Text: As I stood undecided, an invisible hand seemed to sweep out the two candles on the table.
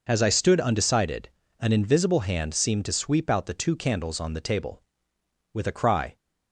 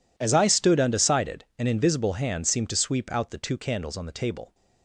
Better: second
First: goes on to say "With a cry"; noticeable; from 5.5 s on; 0.64 s long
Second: none

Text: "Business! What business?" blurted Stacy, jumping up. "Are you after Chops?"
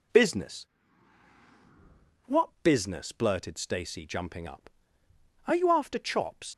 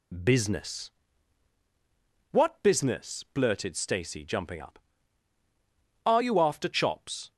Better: second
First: leaves "Chops" unfinished; at 6.5 s; 70 ms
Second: none

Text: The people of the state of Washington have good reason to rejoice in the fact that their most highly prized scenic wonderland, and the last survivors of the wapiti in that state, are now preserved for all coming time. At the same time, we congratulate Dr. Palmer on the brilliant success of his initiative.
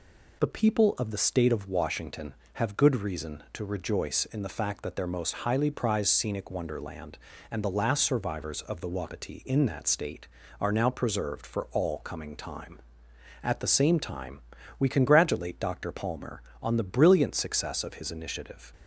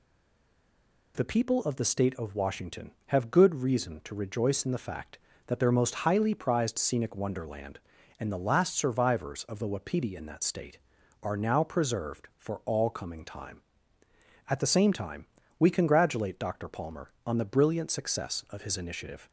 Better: first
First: none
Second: stays silent before the first word; until 1.1 s; 1.1 s long

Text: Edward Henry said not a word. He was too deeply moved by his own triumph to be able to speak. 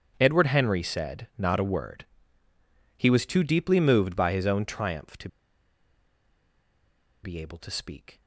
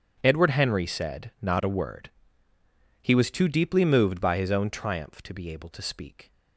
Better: second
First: starts louder than the rest; strong; until 1.2 s; 8 dB // pauses between "to" and "be"; strong; at 5.2 s; 1.9 s long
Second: starts louder than the rest; strong; until 1.2 s; 8.5 dB

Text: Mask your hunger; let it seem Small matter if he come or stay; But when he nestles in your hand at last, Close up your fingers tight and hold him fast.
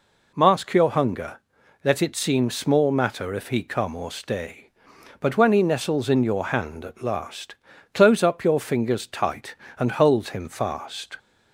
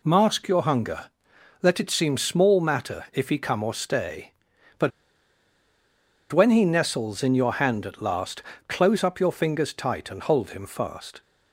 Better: first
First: none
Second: pauses between "But" and "when"; strong; at 4.9 s; 1.4 s long

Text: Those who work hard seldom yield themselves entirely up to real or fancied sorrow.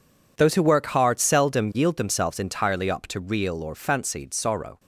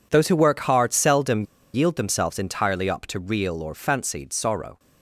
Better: first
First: none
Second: pauses between "seldom" and "yield"; slight; at 1.4 s; 0.31 s long

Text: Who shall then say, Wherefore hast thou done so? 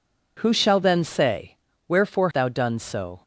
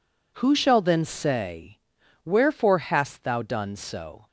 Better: second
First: skips "hast"; at 2.3 s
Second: none

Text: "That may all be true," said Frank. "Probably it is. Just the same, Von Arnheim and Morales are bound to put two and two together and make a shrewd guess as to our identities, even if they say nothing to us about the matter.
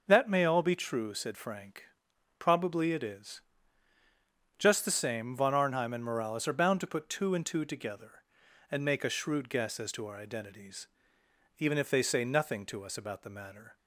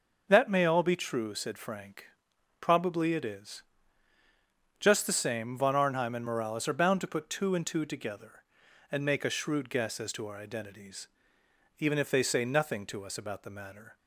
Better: neither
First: starts louder than the rest; until 1.0 s; 6 dB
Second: starts louder than the rest; until 1.3 s; 6 dB

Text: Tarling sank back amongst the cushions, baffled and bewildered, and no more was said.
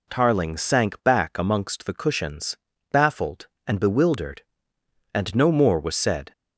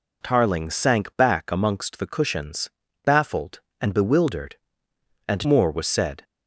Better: first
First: none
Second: skips "no"; at 5.4 s

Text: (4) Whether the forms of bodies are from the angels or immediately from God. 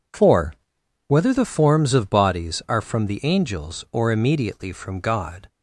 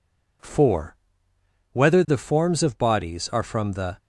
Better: first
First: none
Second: stops before "angels or immediately from God"; at 3.9 s

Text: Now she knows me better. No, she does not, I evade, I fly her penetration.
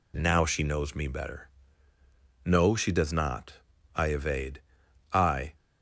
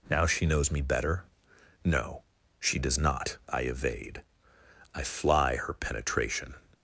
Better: second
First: stops before "fly her penetration"; at 5.5 s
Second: none

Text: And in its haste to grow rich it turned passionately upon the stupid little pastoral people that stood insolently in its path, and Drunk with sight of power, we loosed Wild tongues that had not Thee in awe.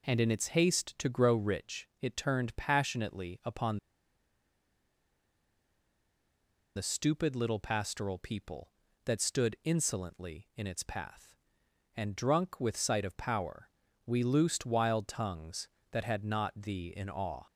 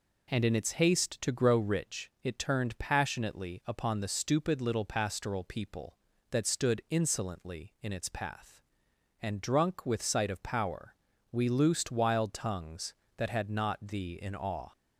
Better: second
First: pauses between "upon" and "the"; strong; at 3.7 s; 2.9 s long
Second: none

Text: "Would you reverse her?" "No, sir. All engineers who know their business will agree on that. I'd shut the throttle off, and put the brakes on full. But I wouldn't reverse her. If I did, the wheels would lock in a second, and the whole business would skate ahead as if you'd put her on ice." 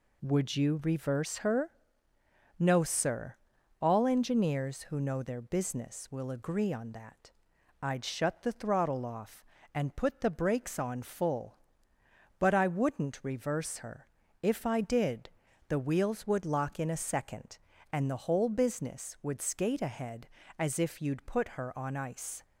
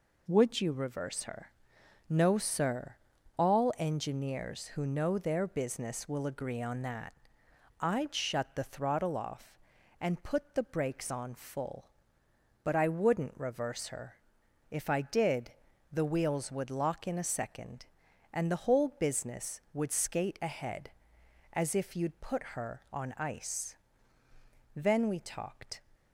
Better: first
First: none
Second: goes on to say "Then we talked"; noticeable; from 24.7 s on; 1.0 s long

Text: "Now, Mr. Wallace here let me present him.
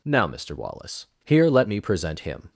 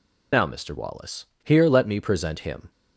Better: first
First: pauses between "Wallace" and "here"; slight; at 1.0 s; 0.18 s long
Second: loses the start of "Now"; at 0.3 s; 90 ms // pauses between "Wallace" and "here"; slight; at 1.2 s; 0.18 s long

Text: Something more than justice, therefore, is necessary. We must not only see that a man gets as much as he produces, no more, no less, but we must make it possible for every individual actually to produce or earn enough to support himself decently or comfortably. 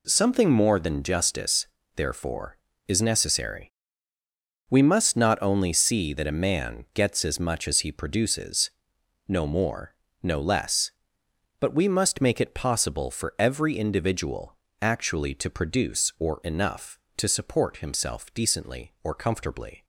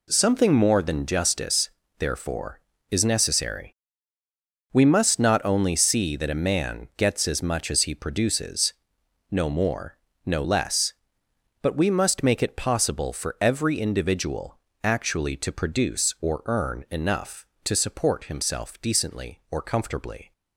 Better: second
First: pauses between "individual" and "actually"; slight; at 14.5 s; 0.26 s long // skips "earn"; at 16.4 s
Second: pauses between "individual" and "actually"; slight; at 14.5 s; 0.26 s long

